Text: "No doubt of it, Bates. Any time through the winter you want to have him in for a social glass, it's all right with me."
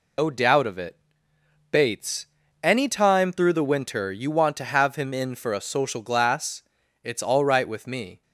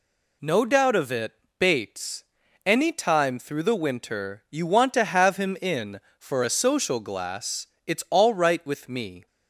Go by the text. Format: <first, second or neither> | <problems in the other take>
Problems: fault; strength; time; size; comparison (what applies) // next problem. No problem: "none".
second | loses the start of "No"; at 0.1 s; 55 ms